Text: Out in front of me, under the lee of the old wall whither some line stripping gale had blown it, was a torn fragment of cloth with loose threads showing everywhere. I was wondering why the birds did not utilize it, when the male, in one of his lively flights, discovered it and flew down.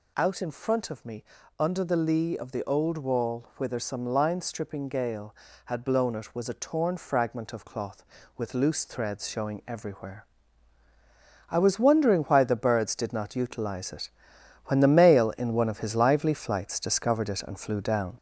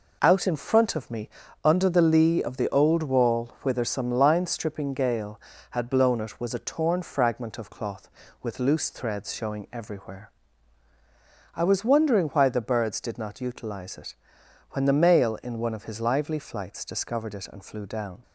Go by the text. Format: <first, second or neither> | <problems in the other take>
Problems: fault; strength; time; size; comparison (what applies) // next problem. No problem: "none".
second | gets louder; throughout; 3.5 dB